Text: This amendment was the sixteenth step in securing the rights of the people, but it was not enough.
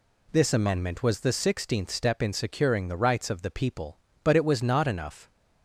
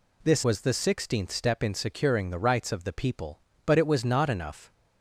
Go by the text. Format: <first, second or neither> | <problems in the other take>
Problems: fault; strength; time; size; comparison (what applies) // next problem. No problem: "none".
first | skips "amendment"; at 0.4 s